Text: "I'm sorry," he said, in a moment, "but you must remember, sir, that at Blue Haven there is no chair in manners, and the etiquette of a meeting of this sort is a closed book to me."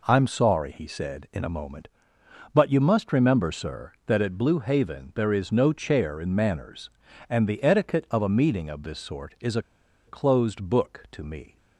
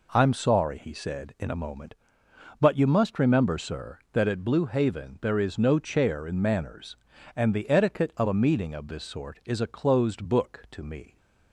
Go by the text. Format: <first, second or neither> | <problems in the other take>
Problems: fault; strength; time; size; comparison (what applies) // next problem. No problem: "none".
second | pauses between "a" and "closed"; at 9.6 s; 0.44 s long